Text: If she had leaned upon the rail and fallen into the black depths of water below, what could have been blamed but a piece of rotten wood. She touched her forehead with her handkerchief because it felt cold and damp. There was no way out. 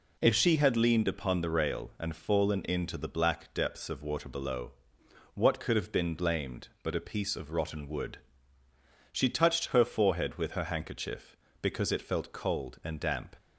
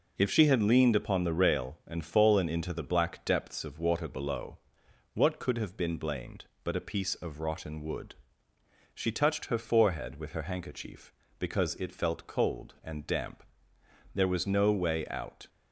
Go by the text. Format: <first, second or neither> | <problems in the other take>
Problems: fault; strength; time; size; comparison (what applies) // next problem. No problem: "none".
second | stops before "There was no way out"; at 13.3 s